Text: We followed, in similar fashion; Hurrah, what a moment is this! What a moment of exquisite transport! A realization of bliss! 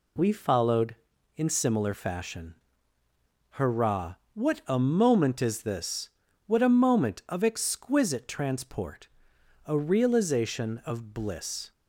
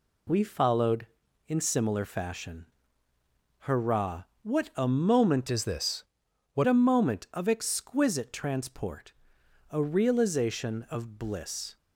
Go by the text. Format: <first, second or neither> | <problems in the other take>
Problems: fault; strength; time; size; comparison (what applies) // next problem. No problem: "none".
first | changes voice from "is" to "What"; from 5.5 to 6.6 s; 1.1 s long